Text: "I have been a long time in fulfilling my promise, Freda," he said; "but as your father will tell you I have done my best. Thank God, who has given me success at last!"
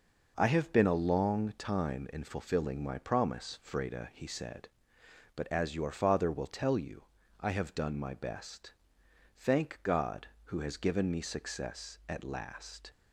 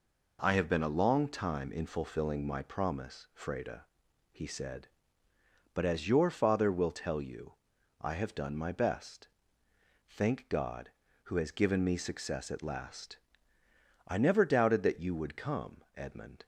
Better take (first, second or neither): first